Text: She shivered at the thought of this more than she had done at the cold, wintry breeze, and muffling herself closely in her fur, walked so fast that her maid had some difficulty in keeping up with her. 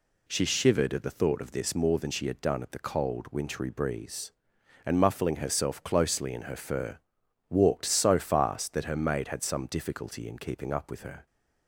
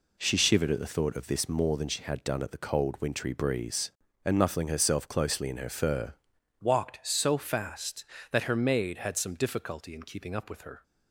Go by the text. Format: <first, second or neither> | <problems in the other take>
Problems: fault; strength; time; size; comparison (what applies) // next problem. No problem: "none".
first | changes voice at "walked"; from 6.6 s on; 4.2 s long